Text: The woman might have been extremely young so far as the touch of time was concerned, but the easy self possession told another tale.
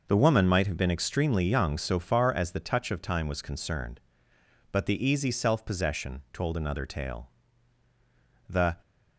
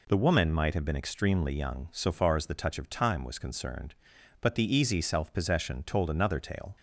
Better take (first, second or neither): second